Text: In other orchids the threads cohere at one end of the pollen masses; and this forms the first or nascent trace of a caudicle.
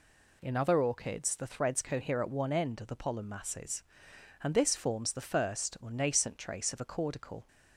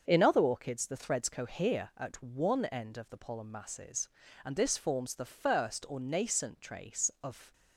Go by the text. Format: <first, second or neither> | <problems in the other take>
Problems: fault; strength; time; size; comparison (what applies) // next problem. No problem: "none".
first | starts louder than the rest; until 1.0 s; 6.5 dB // stops before "a caudicle"; at 7.5 s